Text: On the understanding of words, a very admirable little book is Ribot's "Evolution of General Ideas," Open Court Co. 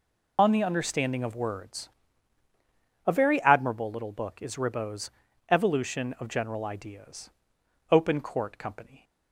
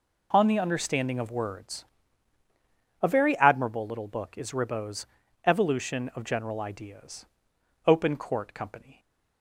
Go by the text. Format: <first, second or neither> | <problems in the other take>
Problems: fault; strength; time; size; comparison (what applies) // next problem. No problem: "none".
second | loses the start of "On"; at 0.3 s; 45 ms // pauses between "Ribot's" and "Evolution"; at 5.0 s; 0.40 s long; also in the second